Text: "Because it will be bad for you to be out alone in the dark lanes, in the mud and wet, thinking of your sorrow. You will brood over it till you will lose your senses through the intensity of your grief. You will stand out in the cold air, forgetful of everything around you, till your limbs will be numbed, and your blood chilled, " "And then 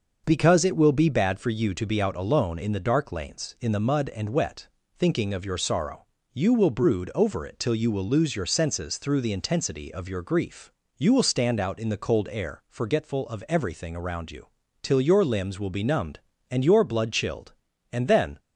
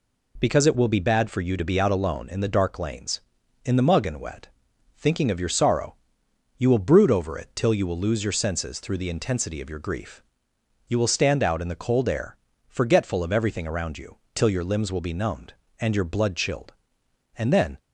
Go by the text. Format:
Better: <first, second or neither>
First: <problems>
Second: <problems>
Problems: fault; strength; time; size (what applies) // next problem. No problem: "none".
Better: first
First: none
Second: says "mug" for "mud"; at 3.8 s